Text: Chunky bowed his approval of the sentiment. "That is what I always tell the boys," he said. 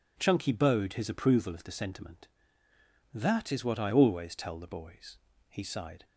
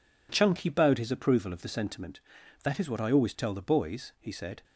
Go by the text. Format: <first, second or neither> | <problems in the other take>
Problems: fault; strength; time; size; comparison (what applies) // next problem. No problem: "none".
second | says "sighed" for "said"; at 5.6 s